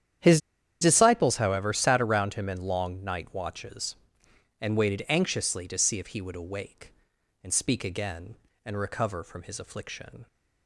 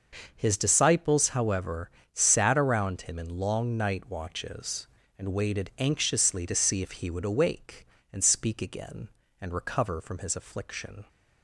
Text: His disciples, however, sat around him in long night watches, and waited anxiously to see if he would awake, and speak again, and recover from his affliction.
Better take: second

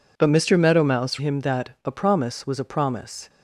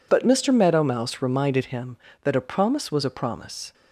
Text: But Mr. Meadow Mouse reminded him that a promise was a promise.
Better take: second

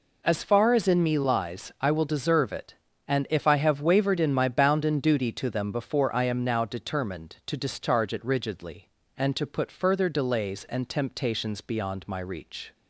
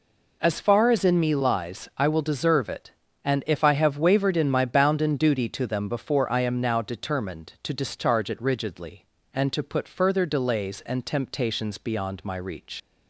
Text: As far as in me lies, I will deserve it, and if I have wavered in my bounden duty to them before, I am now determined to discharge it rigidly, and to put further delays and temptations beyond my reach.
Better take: first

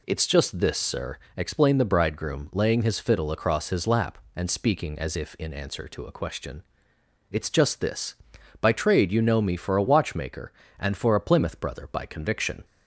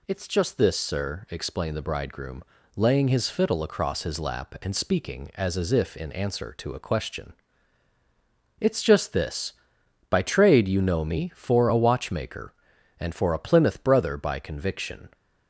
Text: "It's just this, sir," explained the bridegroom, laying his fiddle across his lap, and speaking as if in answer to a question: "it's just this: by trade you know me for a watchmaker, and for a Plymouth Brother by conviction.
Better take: first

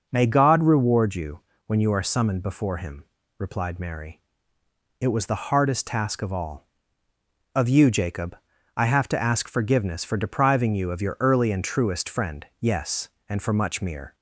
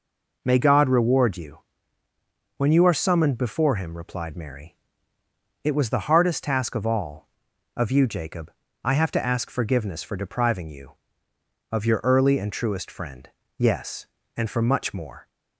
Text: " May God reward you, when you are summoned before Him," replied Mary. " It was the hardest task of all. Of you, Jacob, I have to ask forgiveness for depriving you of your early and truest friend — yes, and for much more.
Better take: second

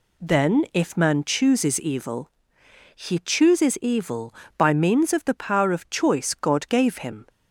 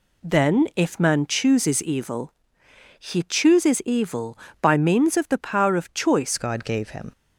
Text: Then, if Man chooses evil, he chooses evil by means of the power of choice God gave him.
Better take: first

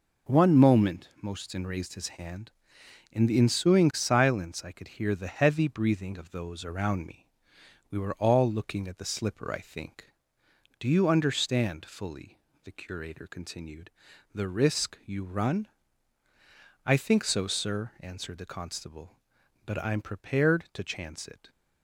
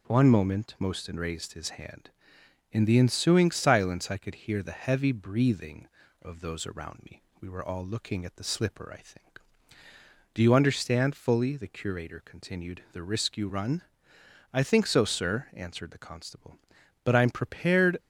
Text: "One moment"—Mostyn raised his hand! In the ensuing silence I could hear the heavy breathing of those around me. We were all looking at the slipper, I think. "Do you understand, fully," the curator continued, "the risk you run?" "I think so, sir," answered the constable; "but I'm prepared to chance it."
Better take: first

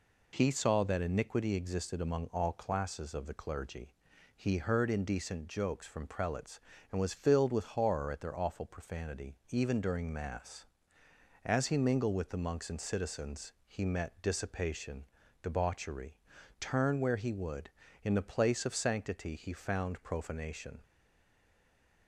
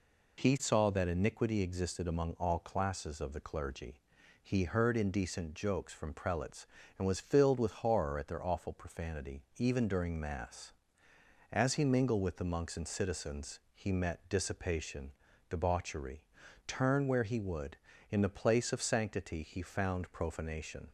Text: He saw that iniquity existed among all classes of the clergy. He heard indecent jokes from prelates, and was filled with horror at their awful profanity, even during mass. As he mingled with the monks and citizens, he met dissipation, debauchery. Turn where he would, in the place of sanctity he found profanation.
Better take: second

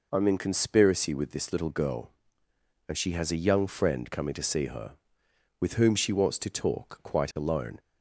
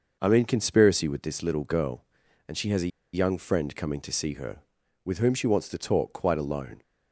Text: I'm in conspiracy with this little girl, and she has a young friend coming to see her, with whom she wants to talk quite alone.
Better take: first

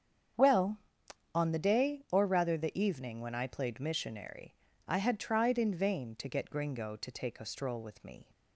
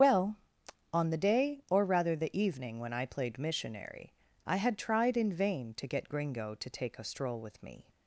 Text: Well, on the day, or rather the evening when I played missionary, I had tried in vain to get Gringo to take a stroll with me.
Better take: first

